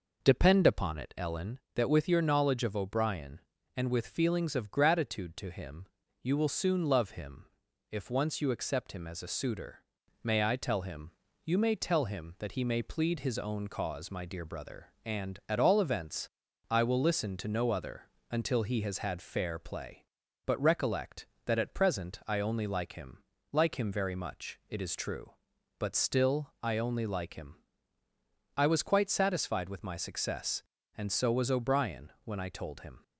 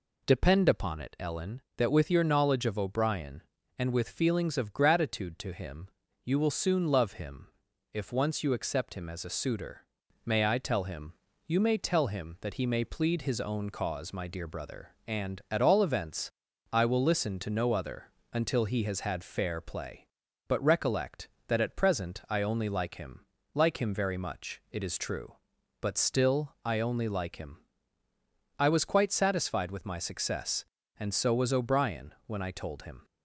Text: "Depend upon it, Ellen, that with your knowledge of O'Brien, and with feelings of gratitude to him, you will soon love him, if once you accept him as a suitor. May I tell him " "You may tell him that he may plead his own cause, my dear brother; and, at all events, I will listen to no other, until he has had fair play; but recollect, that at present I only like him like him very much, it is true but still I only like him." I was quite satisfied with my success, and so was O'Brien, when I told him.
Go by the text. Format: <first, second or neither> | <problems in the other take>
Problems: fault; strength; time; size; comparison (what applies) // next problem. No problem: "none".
second | starts louder than the rest; noticeable; until 1.7 s; 5 dB // pauses between "him" and "like"; slight; at 23.2 s; 0.30 s long; slight in the second